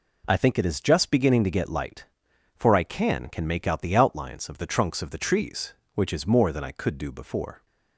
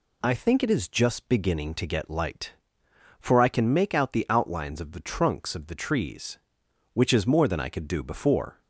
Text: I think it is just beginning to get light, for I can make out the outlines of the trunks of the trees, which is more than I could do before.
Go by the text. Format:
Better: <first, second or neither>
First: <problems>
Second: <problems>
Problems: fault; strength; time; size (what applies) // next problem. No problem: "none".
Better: second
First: says "can" twice; at 3.2 s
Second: none